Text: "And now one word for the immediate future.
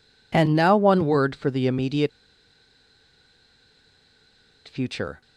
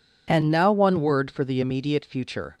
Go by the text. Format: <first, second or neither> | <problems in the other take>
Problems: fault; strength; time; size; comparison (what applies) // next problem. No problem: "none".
second | pauses between "immediate" and "future"; strong; at 2.1 s; 2.5 s long